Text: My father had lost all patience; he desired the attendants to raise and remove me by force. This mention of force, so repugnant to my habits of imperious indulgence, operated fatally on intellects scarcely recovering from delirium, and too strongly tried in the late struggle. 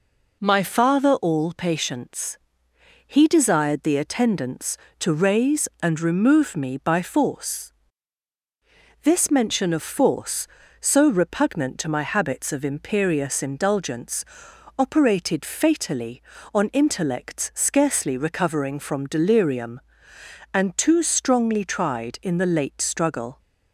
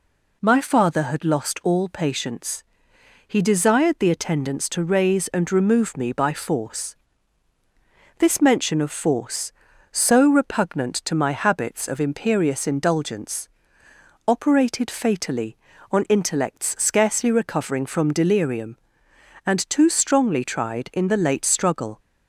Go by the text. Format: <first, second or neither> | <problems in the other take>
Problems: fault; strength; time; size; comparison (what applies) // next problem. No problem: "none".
second | skips "had lost"; at 1.1 s